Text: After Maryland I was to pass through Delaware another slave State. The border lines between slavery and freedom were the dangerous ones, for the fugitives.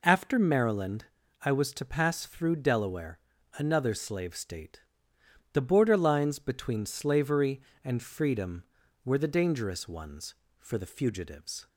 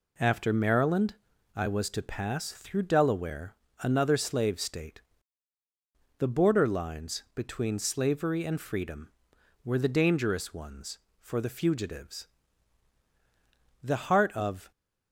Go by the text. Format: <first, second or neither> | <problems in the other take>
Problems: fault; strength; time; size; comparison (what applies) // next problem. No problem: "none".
first | pauses between "Maryland" and "I"; at 1.1 s; 0.40 s long; slight in the first // pauses between "Delaware" and "another"; slight; at 3.5 s; 0.26 s long; slight in the first // goes on to say "The heart of"; noticeable; from 13.8 s on; 0.88 s long